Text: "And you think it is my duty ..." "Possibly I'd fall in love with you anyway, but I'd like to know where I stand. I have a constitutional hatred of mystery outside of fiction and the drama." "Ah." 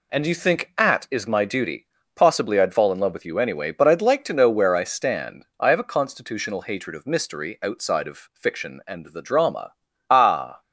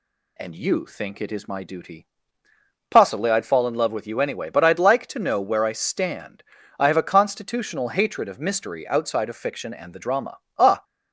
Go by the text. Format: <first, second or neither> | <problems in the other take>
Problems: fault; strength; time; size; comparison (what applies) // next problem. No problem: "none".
second | says "at" for "it"; at 0.7 s